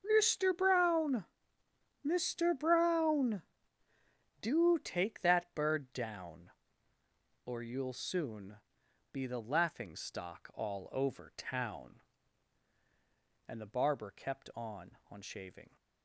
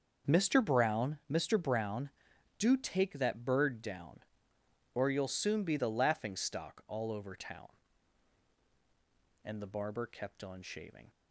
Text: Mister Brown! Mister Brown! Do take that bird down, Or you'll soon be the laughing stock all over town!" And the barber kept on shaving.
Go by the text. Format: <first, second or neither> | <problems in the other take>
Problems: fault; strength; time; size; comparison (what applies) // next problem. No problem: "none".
second | starts louder than the rest; until 1.0 s; 7 dB; also in the second // pauses between "soon" and "be"; noticeable; at 8.5 s; 0.55 s long // says "on" twice; at 15.0 s